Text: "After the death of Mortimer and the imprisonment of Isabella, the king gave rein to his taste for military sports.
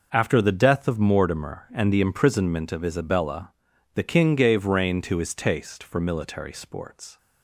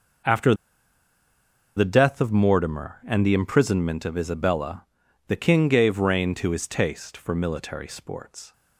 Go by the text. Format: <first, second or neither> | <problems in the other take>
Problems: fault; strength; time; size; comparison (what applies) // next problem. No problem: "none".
first | pauses between "After" and "the"; at 0.5 s; 1.2 s long